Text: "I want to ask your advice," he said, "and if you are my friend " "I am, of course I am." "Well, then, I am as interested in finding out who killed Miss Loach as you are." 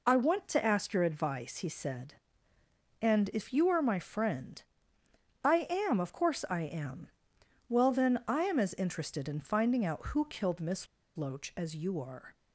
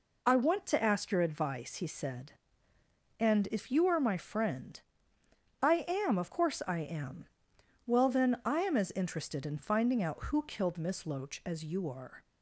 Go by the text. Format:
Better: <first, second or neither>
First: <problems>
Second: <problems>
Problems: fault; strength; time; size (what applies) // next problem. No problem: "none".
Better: second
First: pauses between "Miss" and "Loach"; slight; at 10.8 s; 0.30 s long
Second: none